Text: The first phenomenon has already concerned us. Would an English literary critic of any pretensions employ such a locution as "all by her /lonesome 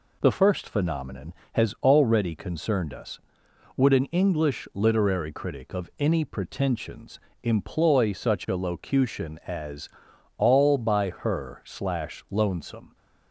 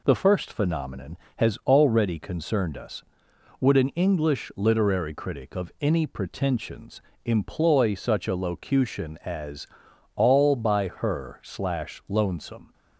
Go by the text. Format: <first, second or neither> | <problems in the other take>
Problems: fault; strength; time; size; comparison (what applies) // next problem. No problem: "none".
neither | pauses between "pretensions" and "employ"; slight; the same in both // pauses between "as" and "all"; noticeable; the same in both